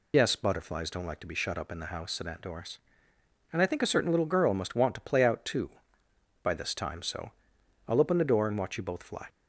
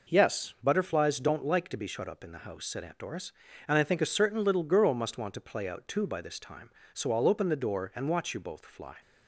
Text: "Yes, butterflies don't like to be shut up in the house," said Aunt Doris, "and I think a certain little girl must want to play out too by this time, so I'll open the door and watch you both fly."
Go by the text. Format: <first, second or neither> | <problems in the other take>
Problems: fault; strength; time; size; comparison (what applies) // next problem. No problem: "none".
second | loses the start of "Yes"; at 0.1 s; 45 ms // pauses between "so" and "I'll"; noticeable; at 7.3 s; 0.56 s long